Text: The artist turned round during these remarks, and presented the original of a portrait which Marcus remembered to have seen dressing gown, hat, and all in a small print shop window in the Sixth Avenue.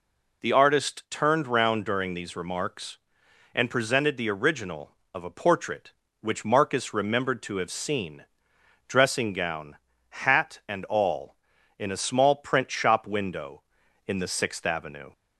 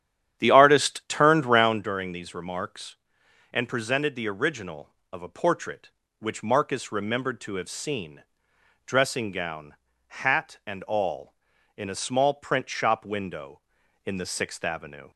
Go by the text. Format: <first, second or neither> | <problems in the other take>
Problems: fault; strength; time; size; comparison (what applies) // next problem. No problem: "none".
first | starts louder than the rest; strong; until 1.9 s; 10 dB // pauses between "seen" and "dressing"; noticeable; at 8.2 s; 0.60 s long; noticeable in the first